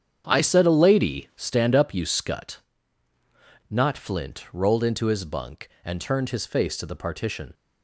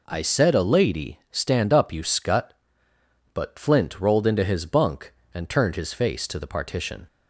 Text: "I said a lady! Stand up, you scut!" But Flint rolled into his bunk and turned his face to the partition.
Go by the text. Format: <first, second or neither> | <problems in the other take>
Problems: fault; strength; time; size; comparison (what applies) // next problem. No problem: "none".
second | starts louder than the rest; strong; until 1.2 s; 8 dB // says "Not" for "But"; at 3.6 s